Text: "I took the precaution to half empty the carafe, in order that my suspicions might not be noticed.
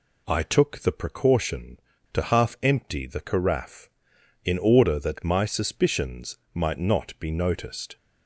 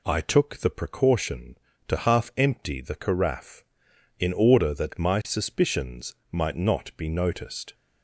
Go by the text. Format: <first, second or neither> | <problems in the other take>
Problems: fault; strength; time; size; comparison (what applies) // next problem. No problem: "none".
neither | pauses between "suspicions" and "might"; slight; the same in both